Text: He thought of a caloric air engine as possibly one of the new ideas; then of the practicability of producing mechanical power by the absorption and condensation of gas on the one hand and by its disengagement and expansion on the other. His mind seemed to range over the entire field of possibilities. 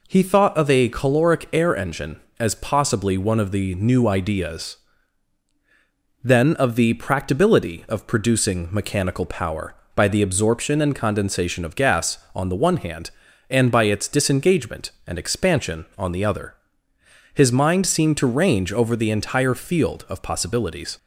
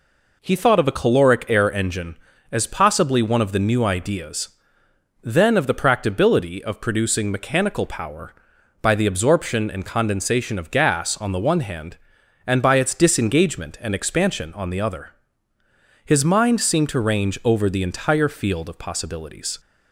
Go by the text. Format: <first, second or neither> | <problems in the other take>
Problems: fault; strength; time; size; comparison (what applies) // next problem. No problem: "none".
neither | none